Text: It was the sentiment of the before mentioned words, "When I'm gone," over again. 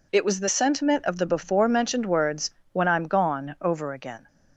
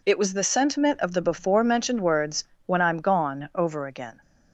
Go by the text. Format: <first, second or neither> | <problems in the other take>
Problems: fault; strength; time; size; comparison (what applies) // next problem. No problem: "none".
neither | none